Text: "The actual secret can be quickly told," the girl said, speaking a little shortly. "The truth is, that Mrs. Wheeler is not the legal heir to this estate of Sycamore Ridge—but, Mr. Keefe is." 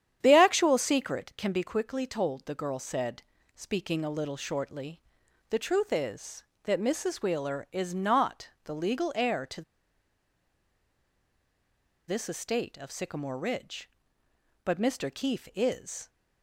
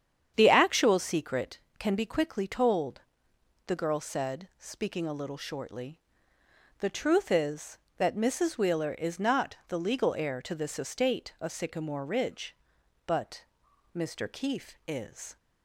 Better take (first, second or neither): second